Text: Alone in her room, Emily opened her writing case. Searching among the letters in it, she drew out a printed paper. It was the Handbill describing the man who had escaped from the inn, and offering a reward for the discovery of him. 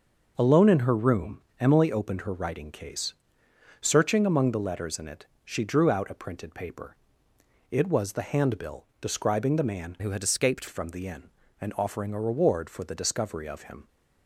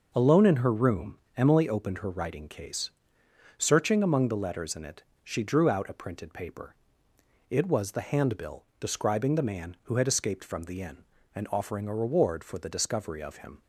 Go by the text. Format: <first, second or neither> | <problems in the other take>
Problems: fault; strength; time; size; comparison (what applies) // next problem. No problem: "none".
second | starts louder than the rest; noticeable; until 1.3 s; 6 dB // changes voice from "who" to "escaped"; from 9.9 to 10.6 s; 0.7 s long